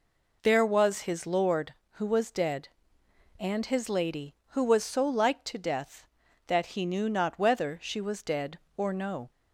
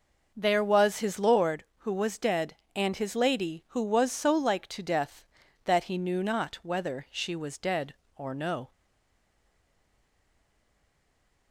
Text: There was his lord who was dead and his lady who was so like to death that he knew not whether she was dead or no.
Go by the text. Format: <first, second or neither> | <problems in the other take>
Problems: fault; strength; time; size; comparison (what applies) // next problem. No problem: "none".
first | stays silent after the last word; strong; from 8.7 s on; 2.8 s long